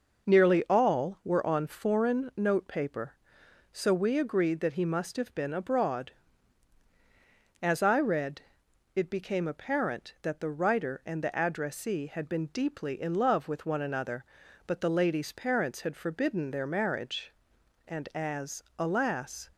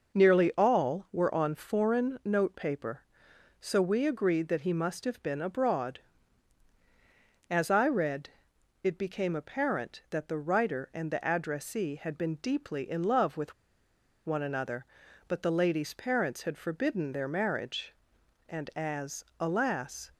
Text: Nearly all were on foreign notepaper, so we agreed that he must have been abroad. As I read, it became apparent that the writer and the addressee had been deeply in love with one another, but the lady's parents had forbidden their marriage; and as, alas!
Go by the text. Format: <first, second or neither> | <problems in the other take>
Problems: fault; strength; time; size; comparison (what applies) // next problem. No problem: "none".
first | pauses between "with" and "one"; noticeable; at 13.5 s; 0.73 s long